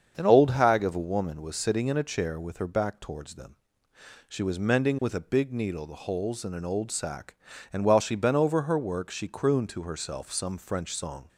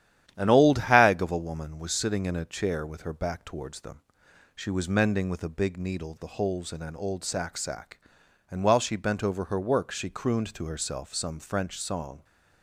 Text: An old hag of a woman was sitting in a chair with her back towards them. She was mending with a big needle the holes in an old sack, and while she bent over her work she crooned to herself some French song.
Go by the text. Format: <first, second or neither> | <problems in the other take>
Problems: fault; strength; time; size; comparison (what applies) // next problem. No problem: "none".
first | starts louder than the rest; strong; until 1.3 s; 11 dB; strong in the first // says "sack" twice; at 7.5 s